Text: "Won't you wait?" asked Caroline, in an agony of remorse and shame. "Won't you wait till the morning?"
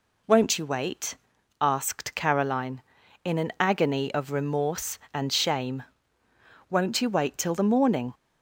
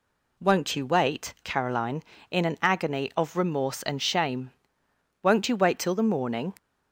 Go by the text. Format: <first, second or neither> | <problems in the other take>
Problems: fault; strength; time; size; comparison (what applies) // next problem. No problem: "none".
first | skips "asked"; at 1.3 s